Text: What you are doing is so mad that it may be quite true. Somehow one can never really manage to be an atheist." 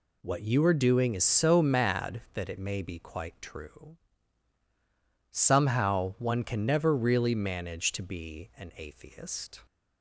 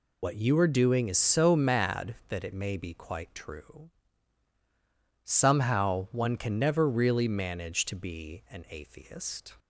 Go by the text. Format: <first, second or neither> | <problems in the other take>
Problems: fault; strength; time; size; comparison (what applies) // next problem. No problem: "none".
first | loses the start of "What"; at 0.2 s; 65 ms